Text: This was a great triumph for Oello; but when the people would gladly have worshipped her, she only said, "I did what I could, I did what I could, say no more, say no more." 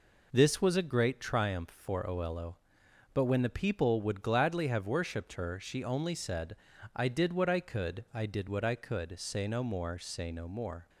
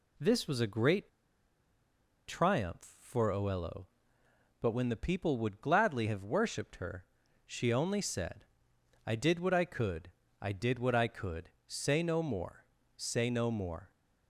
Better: first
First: none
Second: pauses between "great" and "triumph"; at 1.0 s; 1.1 s long

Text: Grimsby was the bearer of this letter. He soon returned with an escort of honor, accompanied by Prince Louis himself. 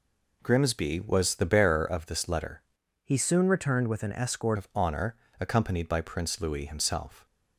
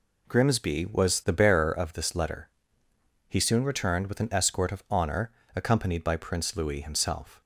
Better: second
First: changes voice from "He" to "escort"; from 3.0 to 4.5 s; 1.5 s long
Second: none

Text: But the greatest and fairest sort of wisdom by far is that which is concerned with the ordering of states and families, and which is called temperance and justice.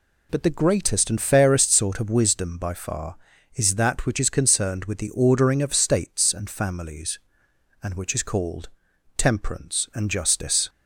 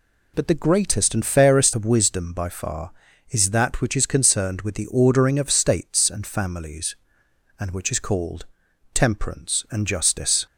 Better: first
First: pauses between "called" and "temperance"; noticeable; at 8.6 s; 0.48 s long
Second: skips "sort"; at 1.7 s // pauses between "called" and "temperance"; noticeable; at 8.4 s; 0.48 s long

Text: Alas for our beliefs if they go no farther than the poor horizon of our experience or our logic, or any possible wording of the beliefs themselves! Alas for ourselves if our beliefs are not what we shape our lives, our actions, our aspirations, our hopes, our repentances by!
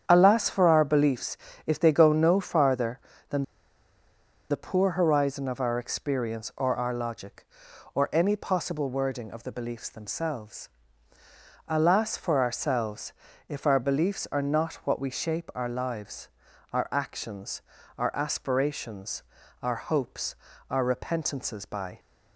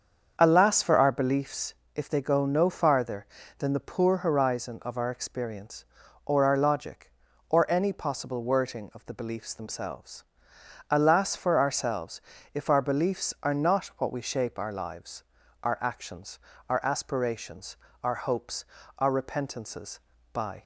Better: second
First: starts louder than the rest; strong; until 1.0 s; 8.5 dB // pauses between "beliefs" and "if"; slight; at 1.3 s; 0.30 s long // pauses between "than" and "the"; at 3.4 s; 1.0 s long // pauses between "ourselves" and "if"; at 13.1 s; 0.38 s long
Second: starts louder than the rest; until 1.4 s; 7 dB // pauses between "beliefs" and "if"; slight; at 1.7 s; 0.20 s long // pauses between "ourselves" and "if"; slight; at 12.2 s; 0.32 s long

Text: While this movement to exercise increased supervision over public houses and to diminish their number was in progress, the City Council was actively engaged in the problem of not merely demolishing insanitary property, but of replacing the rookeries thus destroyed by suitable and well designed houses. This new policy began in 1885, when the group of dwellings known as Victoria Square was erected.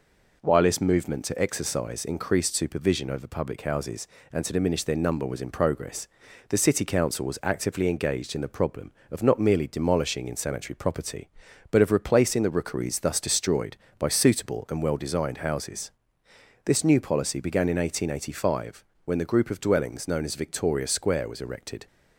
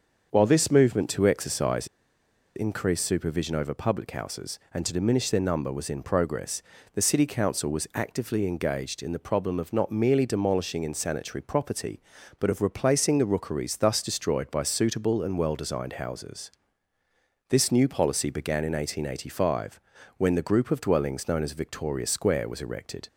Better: first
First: none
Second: starts louder than the rest; until 1.3 s; 6.5 dB // pauses between "exercise" and "increased"; noticeable; at 1.8 s; 0.68 s long

